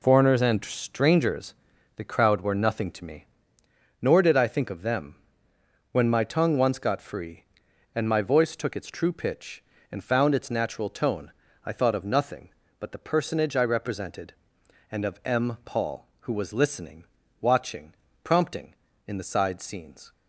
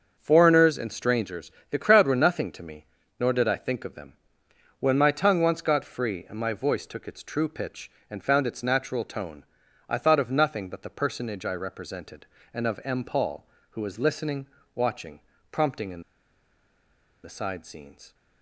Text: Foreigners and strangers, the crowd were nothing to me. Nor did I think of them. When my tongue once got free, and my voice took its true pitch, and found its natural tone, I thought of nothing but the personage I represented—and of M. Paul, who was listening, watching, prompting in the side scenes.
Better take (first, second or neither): first